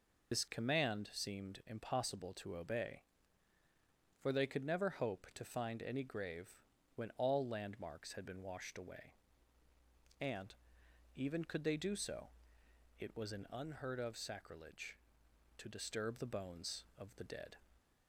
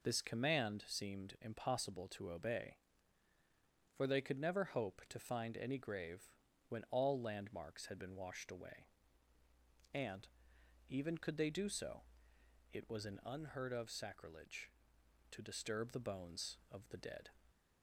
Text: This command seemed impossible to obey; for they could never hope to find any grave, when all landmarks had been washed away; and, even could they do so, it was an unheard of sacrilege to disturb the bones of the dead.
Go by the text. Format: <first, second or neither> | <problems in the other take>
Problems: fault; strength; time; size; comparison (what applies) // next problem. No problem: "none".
second | loses the start of "This"; at 0.3 s; 55 ms